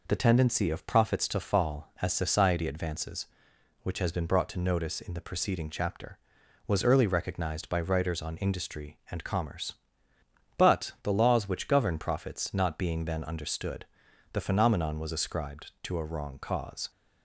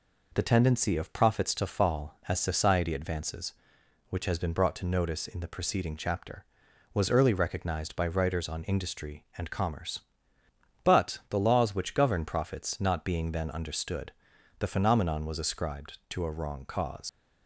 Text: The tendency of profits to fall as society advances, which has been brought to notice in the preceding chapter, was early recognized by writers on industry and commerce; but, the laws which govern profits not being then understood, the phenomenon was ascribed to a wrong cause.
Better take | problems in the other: first | leaves "cause" unfinished; at 17.0 s; 75 ms

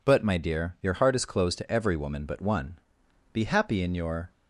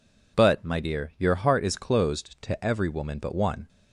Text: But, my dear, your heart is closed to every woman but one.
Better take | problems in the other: second | goes on to say "Be happy in your"; noticeable; from 3.3 s on; 0.98 s long

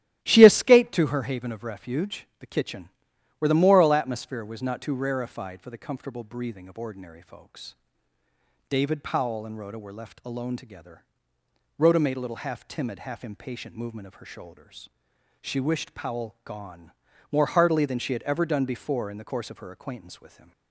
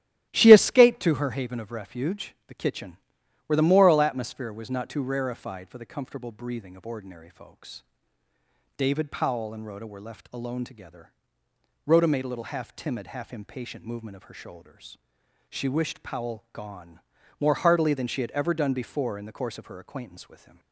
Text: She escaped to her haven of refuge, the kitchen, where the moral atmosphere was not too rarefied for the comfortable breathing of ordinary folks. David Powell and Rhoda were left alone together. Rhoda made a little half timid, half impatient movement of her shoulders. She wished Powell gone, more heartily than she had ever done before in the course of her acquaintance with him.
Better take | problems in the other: neither | starts louder than the rest; strong; the same in both

